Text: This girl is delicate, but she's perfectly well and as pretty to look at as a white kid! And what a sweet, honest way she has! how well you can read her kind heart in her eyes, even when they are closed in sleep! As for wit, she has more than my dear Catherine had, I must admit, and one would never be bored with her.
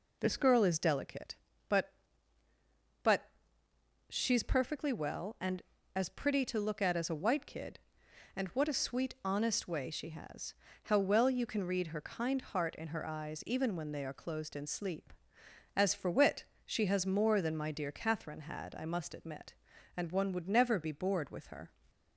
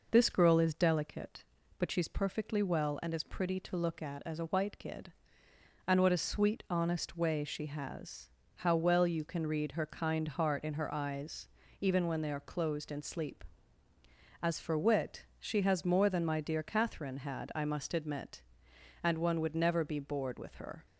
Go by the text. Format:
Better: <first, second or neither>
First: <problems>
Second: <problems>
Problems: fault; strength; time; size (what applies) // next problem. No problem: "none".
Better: second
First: says "but" twice; at 3.0 s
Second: none